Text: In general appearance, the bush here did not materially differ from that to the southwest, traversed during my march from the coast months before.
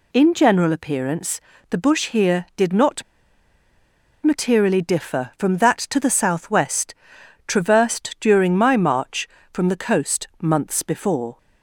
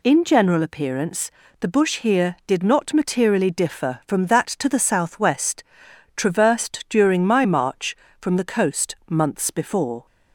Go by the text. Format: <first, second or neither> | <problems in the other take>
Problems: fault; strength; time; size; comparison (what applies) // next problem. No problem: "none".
second | pauses between "not" and "materially"; at 3.0 s; 1.2 s long